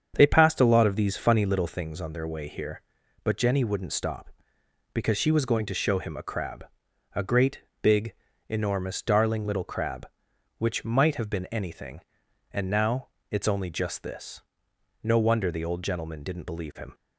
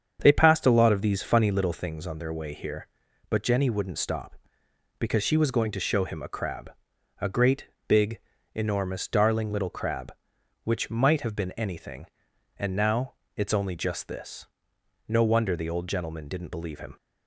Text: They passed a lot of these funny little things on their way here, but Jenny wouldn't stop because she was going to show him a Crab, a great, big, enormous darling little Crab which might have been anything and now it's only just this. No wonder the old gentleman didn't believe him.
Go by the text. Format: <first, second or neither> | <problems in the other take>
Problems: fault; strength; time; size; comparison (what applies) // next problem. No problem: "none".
neither | starts louder than the rest; strong; the same in both // pauses between "now" and "it's"; slight; the same in both